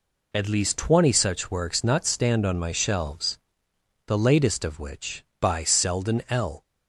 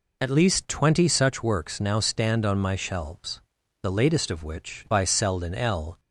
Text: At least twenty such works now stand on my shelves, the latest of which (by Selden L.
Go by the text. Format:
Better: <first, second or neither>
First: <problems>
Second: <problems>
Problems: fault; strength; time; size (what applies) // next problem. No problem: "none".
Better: second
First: says "not" for "now"; at 1.8 s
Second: none